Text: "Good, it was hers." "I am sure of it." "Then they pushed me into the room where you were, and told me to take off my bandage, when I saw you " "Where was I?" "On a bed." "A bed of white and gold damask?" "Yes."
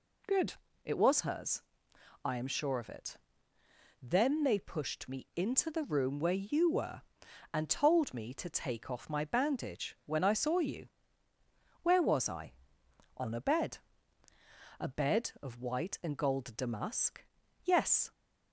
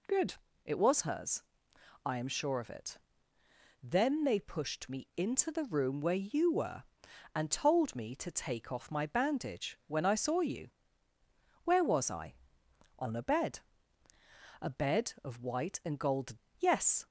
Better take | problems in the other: first | skips "damask"; at 16.4 s

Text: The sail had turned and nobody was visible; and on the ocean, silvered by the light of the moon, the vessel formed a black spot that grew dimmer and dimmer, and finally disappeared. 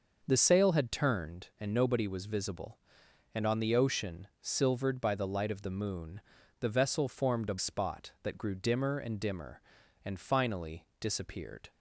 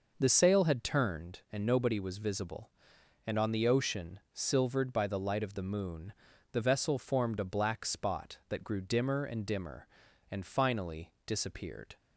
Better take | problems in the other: second | starts louder than the rest; noticeable; until 1.2 s; 6 dB // skips "black"; at 7.5 s

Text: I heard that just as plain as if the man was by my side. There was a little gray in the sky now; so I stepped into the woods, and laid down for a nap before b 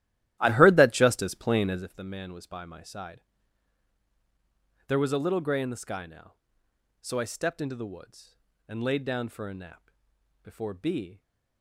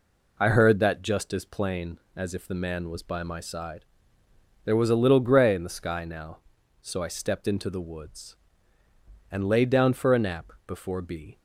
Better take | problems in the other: second | starts louder than the rest; strong; until 1.9 s; 14 dB // pauses between "nap" and "before"; noticeable; at 9.9 s; 0.54 s long

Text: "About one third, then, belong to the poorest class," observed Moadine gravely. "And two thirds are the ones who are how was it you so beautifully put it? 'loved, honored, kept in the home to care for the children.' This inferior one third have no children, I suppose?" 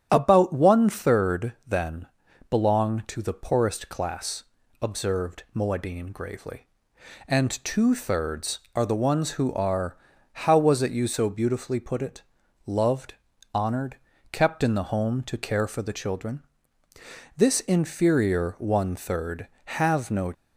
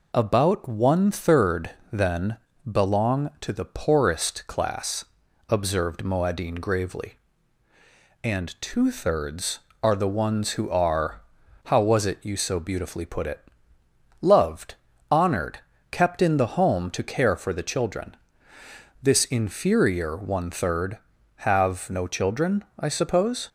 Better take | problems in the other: second | starts louder than the rest; strong; until 1.1 s; 9.5 dB // pauses between "are" and "how"; slight; at 9.9 s; 0.36 s long; also in the second // stops before "children I suppose"; at 20.3 s

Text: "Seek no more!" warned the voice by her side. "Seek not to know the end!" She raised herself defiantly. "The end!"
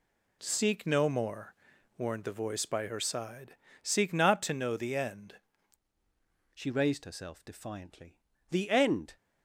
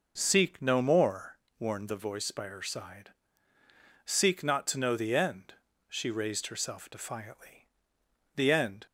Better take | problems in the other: second | changes voice at "She"; from 6.5 s on; 2.6 s long

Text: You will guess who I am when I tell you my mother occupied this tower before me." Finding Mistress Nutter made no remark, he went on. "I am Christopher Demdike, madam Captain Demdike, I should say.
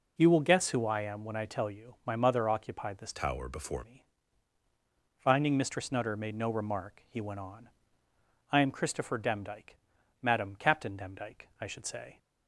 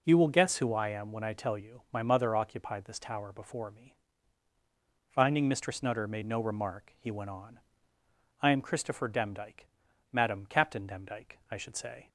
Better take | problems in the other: second | changes voice from "tower" to "before"; from 3.1 to 3.8 s; 0.7 s long

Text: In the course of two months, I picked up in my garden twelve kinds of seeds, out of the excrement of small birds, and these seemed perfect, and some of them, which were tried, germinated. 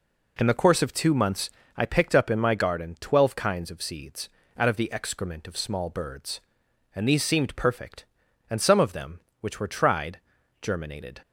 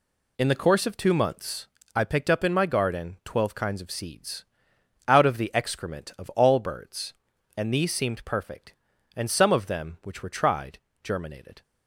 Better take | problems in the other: first | says "all" for "small"; at 6.3 s

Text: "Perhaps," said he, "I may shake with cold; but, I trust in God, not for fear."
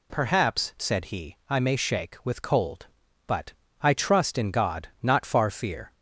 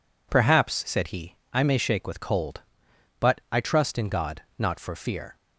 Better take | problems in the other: second | says "far" for "for"; at 5.2 s

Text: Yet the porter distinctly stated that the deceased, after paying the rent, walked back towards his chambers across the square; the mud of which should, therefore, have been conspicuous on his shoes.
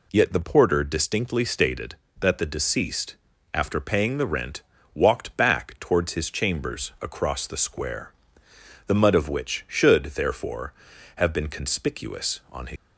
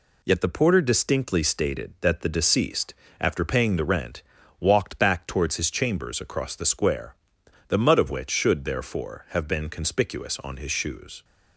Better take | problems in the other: second | stops before "shoes"; at 12.7 s

